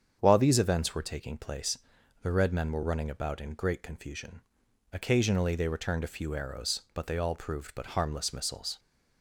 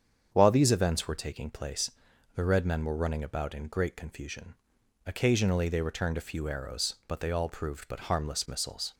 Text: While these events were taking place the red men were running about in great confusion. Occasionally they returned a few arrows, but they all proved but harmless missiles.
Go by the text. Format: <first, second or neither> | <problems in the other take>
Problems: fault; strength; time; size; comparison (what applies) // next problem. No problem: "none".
neither | starts louder than the rest; strong; the same in both // pauses between "place" and "the"; the same in both